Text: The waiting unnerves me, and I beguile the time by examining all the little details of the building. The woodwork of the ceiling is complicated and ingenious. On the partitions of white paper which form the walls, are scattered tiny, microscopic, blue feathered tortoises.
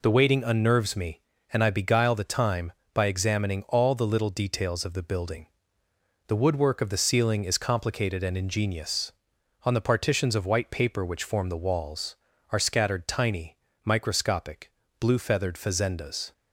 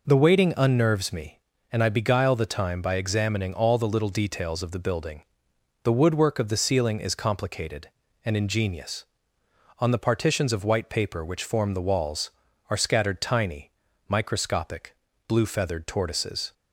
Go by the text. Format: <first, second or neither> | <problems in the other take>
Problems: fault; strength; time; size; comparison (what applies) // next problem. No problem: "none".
second | says "fazendas" for "tortoises"; at 15.5 s